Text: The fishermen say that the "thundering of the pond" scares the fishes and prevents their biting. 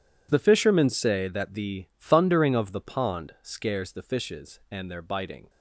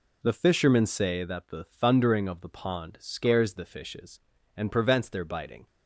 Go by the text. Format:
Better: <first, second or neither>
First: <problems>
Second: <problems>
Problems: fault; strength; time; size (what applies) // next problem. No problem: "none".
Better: second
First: skips "prevents"; at 4.8 s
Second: none